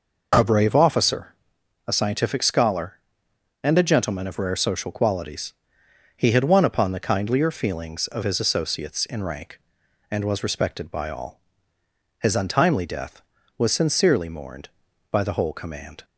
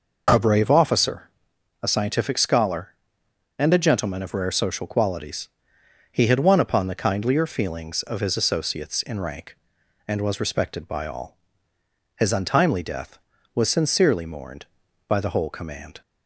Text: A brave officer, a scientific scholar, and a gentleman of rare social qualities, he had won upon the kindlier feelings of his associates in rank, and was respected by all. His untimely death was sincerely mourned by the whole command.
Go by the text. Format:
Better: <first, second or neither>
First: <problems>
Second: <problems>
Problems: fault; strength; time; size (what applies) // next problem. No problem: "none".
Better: neither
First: none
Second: none